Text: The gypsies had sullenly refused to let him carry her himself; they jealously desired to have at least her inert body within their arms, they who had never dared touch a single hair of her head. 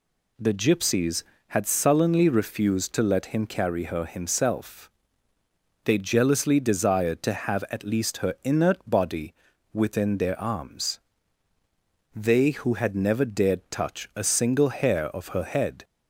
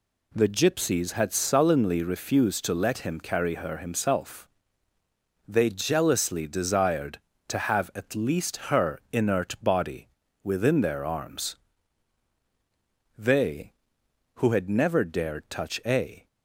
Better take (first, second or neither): first